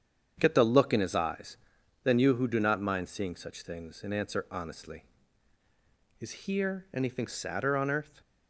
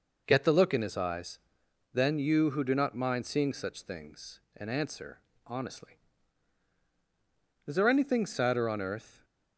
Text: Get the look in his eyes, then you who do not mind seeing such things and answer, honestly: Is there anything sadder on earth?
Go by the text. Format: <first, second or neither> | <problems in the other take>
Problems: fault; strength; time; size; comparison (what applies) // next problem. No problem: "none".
second | starts louder than the rest; strong; until 1.3 s; 8 dB // says "here" for "there"; at 6.4 s